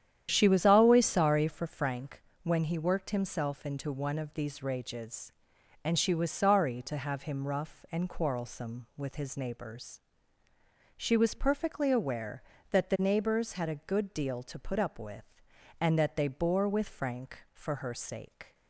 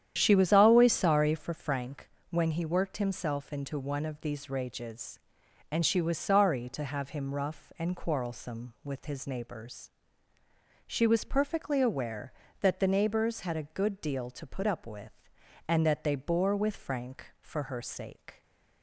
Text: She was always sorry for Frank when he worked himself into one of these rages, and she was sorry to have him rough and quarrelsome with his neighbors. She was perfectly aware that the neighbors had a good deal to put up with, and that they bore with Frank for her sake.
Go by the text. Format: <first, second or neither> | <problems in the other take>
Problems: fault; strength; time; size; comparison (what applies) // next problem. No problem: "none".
neither | starts louder than the rest; strong; the same in both // pauses between "Frank" and "when"; slight; the same in both